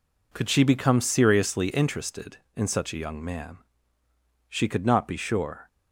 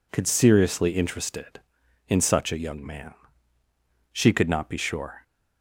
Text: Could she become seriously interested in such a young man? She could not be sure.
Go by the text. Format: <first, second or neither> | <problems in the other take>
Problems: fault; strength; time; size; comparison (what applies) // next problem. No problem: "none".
first | skips "she become"; at 0.2 s